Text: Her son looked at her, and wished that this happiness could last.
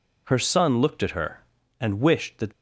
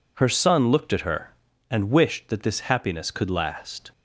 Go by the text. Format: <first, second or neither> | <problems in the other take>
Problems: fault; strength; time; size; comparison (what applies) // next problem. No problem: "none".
second | stops before "this happiness could last"; at 2.5 s